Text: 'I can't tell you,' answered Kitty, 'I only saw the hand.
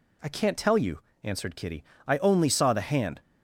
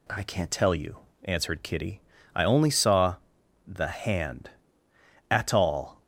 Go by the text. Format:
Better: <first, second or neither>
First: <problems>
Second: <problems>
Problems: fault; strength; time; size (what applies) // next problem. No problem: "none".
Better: first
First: none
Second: pauses between "saw" and "the"; noticeable; at 3.1 s; 0.52 s long // goes on to say "At all"; noticeable; from 5.2 s on; 0.72 s long